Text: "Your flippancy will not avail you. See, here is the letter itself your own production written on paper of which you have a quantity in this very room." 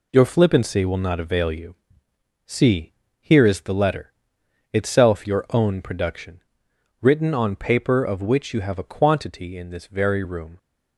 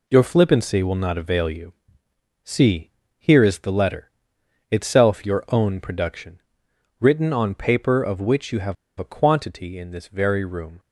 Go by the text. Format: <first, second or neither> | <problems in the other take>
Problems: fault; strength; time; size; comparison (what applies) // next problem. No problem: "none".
first | pauses between "letter" and "itself"; noticeable; at 4.0 s; 0.62 s long; noticeable in the first // pauses between "production" and "written"; noticeable; at 6.4 s; 0.58 s long; noticeable in the first // pauses between "have" and "a"; slight; at 8.7 s; 0.24 s long